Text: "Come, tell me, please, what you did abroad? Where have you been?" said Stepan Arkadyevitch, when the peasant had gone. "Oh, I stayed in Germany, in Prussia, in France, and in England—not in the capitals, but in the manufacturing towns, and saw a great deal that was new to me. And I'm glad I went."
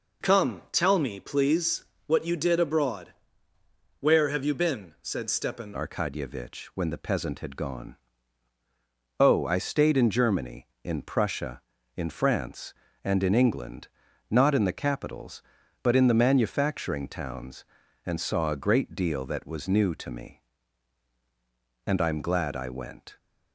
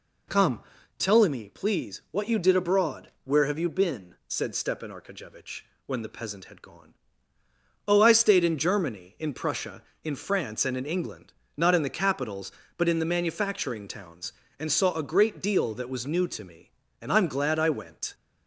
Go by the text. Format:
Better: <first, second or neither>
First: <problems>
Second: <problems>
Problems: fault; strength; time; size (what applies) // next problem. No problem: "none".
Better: second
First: changes voice at "Arkadyevitch"; from 5.7 s on; 17.4 s long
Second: none